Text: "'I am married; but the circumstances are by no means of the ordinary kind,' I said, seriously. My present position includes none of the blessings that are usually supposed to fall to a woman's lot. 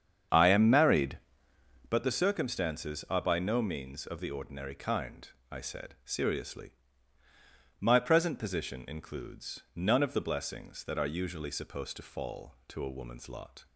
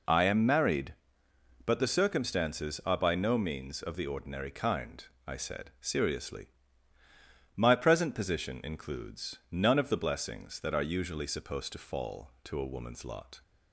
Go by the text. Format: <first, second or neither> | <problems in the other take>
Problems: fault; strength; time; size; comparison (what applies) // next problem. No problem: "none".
second | starts louder than the rest; strong; until 2.0 s; 8 dB // pauses between "includes" and "none"; slight; at 9.6 s; 0.16 s long; slight in the second